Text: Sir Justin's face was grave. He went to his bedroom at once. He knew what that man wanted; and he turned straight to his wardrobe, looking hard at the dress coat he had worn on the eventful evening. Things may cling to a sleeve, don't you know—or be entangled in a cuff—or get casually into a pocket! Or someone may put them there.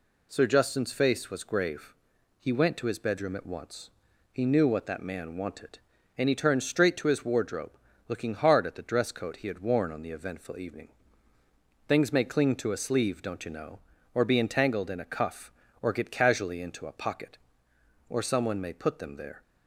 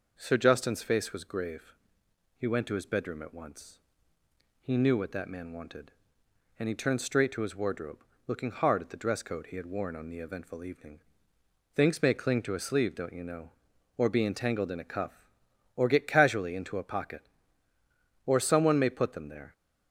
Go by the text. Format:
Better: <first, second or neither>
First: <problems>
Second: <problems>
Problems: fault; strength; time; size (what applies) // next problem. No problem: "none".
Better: neither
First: none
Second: none